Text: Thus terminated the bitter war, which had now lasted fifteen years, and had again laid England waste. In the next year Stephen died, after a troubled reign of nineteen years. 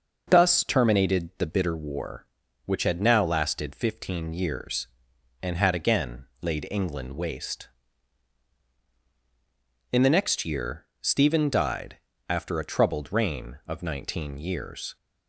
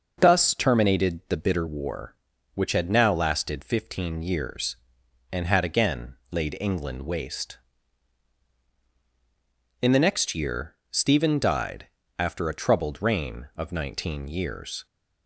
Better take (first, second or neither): neither